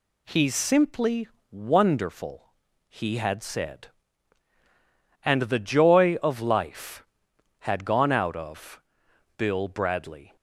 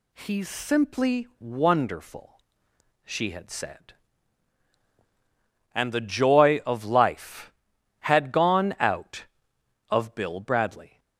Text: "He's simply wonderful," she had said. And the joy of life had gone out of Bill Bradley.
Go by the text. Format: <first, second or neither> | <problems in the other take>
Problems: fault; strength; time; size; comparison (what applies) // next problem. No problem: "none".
second | pauses between "simply" and "wonderful"; slight; at 1.2 s; 0.24 s long // says "he" for "she"; at 2.8 s // pauses between "of" and "Bill"; noticeable; at 8.8 s; 0.56 s long